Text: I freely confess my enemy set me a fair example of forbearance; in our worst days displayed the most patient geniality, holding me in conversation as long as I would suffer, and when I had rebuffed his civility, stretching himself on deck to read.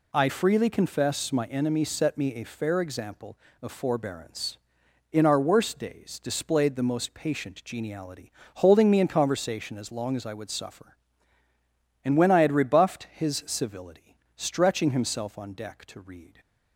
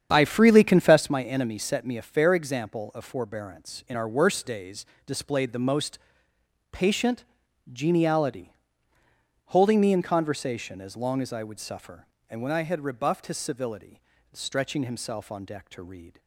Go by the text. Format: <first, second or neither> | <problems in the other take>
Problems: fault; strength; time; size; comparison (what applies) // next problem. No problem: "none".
first | starts louder than the rest; strong; until 1.1 s; 8 dB // pauses between "days" and "displayed"; slight; at 4.8 s; 0.22 s long // pauses between "most" and "patient"; noticeable; at 5.9 s; 0.72 s long // pauses between "patient" and "geniality"; noticeable; at 7.2 s; 0.48 s long